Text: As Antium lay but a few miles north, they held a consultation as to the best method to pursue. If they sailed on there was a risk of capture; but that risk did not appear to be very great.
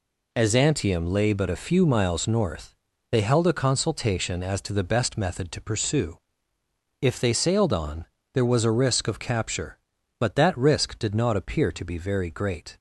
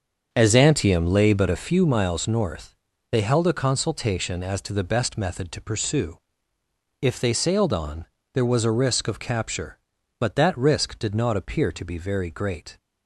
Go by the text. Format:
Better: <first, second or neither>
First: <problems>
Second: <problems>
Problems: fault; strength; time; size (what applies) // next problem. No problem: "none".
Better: first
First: pauses between "on" and "there"; slight; at 8.0 s; 0.28 s long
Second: starts louder than the rest; until 1.7 s; 7 dB // pauses between "on" and "there"; slight; at 8.0 s; 0.28 s long